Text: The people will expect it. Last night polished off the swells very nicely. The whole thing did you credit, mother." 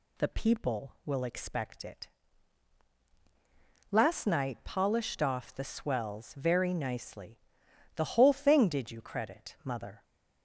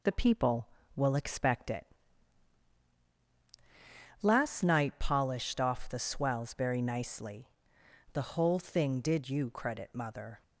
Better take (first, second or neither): neither